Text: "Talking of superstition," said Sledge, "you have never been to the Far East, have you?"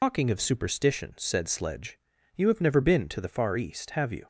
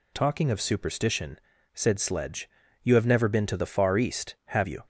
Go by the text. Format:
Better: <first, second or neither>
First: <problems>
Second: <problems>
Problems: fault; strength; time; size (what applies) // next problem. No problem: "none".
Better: second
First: loses the start of "Talking"; at 0.0 s; 95 ms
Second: none